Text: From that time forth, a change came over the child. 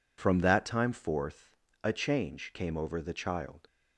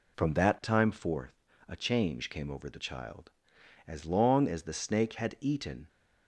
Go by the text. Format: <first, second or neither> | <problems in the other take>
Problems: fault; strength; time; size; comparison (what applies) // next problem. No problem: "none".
first | goes on to say "As long as the snake had eaten"; strong; from 3.8 s on; 2.0 s long